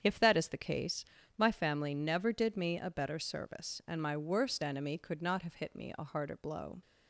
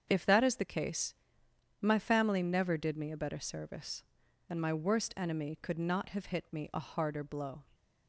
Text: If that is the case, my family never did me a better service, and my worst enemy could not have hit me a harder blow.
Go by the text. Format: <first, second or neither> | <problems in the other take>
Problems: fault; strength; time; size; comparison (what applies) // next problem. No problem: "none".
neither | starts louder than the rest; strong; the same in both